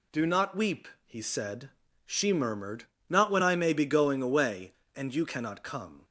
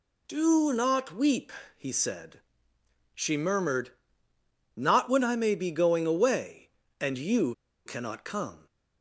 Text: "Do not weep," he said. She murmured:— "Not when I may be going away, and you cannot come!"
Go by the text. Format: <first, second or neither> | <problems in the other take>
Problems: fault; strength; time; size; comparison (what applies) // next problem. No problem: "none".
first | pauses between "you" and "cannot"; slight; at 7.5 s; 0.32 s long